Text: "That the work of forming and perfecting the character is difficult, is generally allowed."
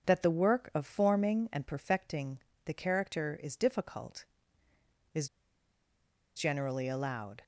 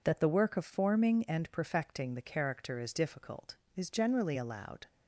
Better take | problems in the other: second | starts louder than the rest; until 1.1 s; 7 dB // pauses between "perfecting" and "the"; slight; at 2.3 s; 0.28 s long // pauses between "is" and "generally"; at 5.2 s; 1.0 s long

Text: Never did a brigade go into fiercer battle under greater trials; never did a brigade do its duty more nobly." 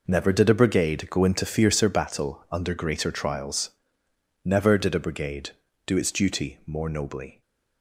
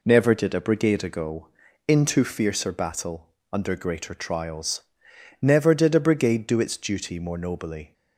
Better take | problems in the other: first | says "ago" for "go"; at 1.0 s // pauses between "battle" and "under"; slight; at 3.2 s; 0.24 s long

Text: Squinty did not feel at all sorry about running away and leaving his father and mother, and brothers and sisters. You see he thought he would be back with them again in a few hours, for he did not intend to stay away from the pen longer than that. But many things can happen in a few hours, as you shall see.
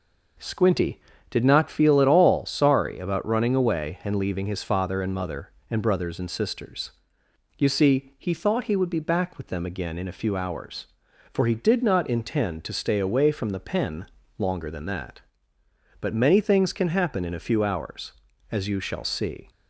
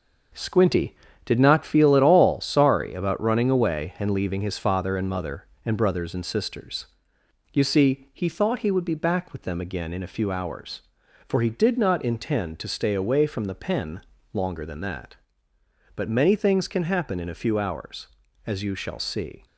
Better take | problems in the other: first | gets quieter; throughout; 6.5 dB // pauses between "pen" and "longer"; slight; at 14.0 s; 0.32 s long; slight in the first

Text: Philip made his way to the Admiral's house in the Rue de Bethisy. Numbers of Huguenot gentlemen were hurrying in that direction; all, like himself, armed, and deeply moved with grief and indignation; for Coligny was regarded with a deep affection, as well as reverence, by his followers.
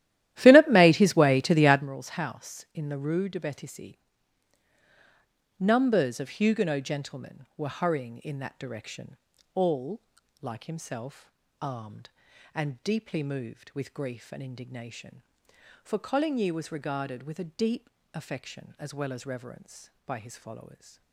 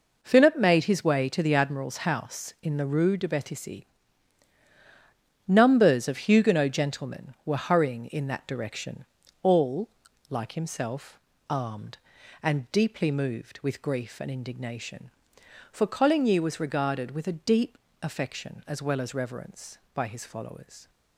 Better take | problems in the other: second | starts louder than the rest; strong; until 1.9 s; 13.5 dB // pauses between "deep" and "affection"; slight; at 17.8 s; 0.24 s long; slight in the second

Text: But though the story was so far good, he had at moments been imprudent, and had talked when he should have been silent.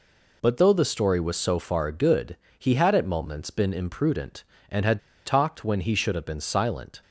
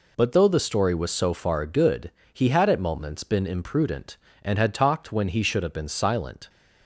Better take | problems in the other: second | pauses between "had" and "talked"; slight; at 4.9 s; 0.26 s long

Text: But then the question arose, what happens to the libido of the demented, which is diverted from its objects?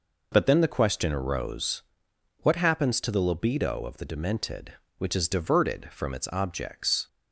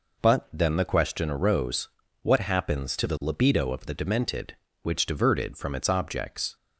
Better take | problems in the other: first | skips "is"; at 5.0 s

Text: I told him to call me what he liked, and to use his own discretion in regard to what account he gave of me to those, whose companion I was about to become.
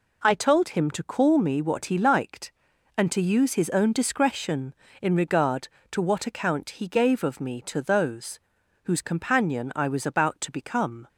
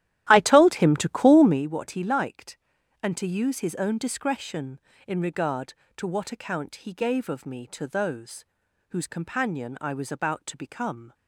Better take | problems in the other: first | starts louder than the rest; strong; until 1.6 s; 13.5 dB

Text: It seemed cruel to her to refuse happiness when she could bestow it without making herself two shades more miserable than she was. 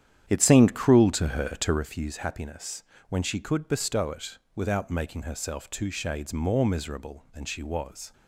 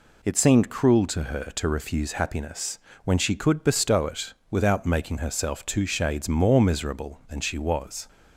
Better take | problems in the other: second | starts louder than the rest; strong; until 1.9 s; 9.5 dB // pauses between "happiness" and "when"; slight; at 2.8 s; 0.26 s long; slight in the second // pauses between "it" and "without"; slight; at 4.3 s; 0.18 s long; slight in the second

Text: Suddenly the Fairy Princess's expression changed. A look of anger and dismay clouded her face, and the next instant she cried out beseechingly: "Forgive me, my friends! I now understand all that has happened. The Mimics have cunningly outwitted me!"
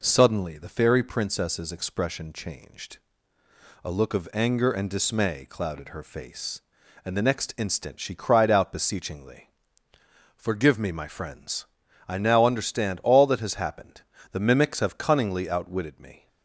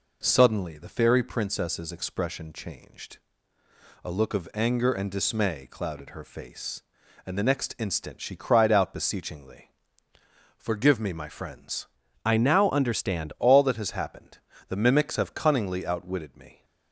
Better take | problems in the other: first | changes voice from "I" to "understand"; from 12.2 to 13.3 s; 1.1 s long

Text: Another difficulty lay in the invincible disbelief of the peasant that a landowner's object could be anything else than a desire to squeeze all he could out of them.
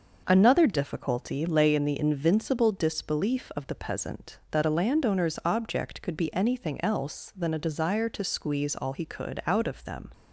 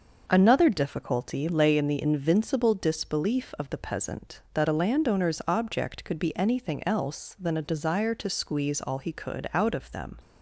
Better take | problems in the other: neither | none

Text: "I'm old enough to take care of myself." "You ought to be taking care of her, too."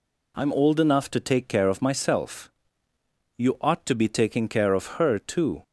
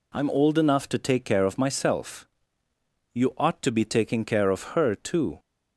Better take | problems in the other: neither | none

